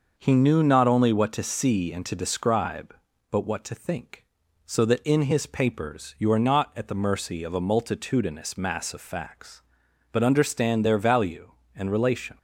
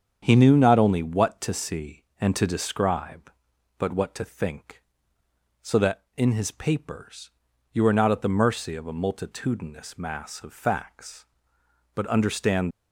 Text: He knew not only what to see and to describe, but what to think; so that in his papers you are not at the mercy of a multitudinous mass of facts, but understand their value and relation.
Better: first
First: none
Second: starts louder than the rest; strong; until 1.2 s; 8 dB // pauses between "papers" and "you"; at 7.2 s; 0.44 s long // stops before "their value and relation"; at 12.7 s

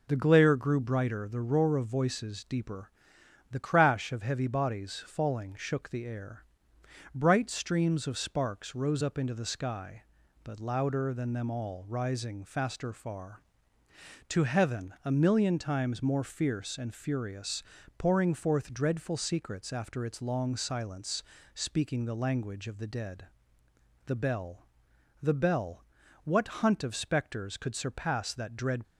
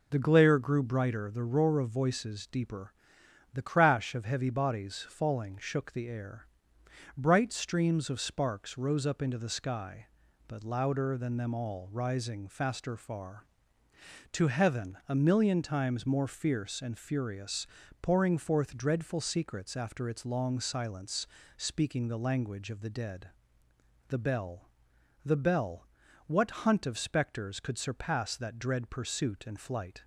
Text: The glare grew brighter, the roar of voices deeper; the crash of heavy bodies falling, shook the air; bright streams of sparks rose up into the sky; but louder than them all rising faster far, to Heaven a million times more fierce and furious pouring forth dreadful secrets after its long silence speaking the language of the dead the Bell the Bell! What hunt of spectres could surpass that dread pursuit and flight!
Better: second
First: pauses between "furious" and "pouring"; slight; at 17.6 s; 0.34 s long // pauses between "silence" and "speaking"; slight; at 21.2 s; 0.32 s long // pauses between "dead" and "the"; noticeable; at 23.2 s; 0.80 s long // pauses between "Bell" and "the"; noticeable; at 24.6 s; 0.52 s long // stops before "pursuit and flight"; at 28.8 s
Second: pauses between "furious" and "pouring"; slight; at 17.6 s; 0.34 s long // pauses between "silence" and "speaking"; slight; at 21.2 s; 0.31 s long // pauses between "dead" and "the"; noticeable; at 23.2 s; 0.80 s long // pauses between "Bell" and "the"; noticeable; at 24.7 s; 0.52 s long

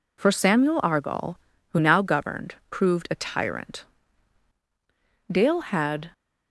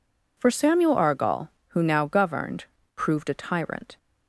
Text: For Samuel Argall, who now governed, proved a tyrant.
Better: second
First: goes on to say "Dale had"; noticeable; from 5.3 s on; 0.78 s long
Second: none

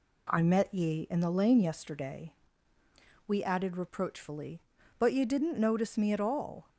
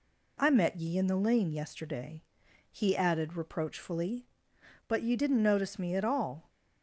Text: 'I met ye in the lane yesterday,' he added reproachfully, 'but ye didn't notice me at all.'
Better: second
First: says "we" for "he"; at 3.2 s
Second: none

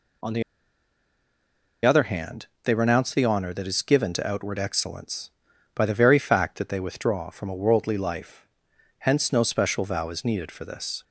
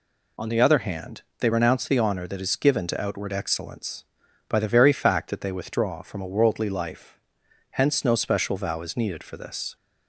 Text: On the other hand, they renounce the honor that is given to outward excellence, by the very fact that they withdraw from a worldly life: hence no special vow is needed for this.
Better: second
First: pauses between "the" and "other"; strong; at 0.4 s; 1.4 s long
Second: none

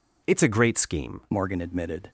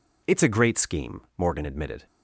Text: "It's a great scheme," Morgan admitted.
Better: second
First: changes voice at "Morgan"; from 1.3 s on; 0.7 s long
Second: none

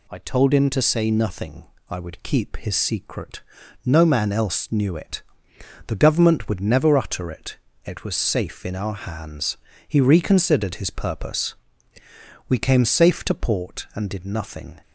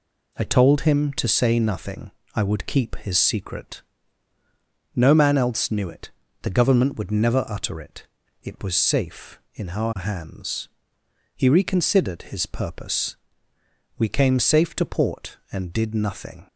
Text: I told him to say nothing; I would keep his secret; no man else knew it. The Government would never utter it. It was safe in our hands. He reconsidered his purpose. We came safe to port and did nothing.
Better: neither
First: none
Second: none

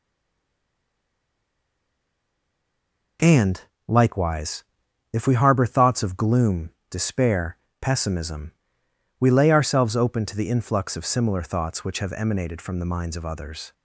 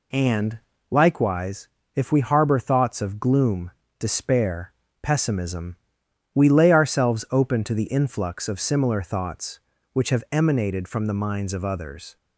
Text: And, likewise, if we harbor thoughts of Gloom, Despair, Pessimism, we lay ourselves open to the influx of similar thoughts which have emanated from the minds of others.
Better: second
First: stays silent before the first word; strong; until 3.1 s; 3.1 s long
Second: none

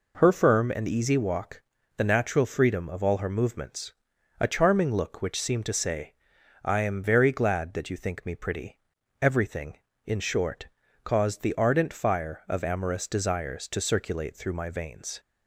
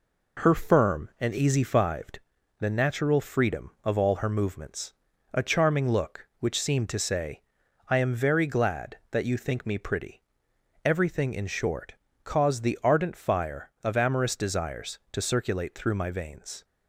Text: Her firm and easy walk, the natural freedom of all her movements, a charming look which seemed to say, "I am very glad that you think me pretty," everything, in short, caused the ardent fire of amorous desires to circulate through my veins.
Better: first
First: none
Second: says "fived" for "walk"; at 1.6 s

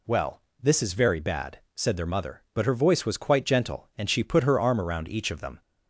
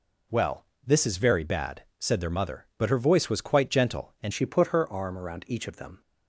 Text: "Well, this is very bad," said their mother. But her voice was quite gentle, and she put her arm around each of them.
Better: first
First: none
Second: changes voice at "she"; from 4.3 s on; 1.7 s long

